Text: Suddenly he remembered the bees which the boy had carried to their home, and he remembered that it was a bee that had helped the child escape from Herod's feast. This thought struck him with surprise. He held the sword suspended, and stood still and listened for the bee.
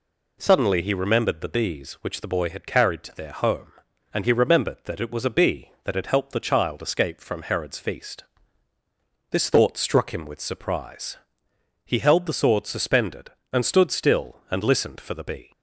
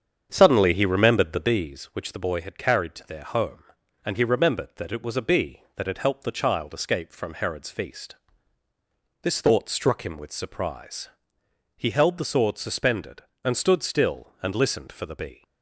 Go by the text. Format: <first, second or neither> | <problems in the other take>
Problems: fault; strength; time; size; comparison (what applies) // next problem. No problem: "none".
first | starts louder than the rest; strong; until 1.7 s; 7.5 dB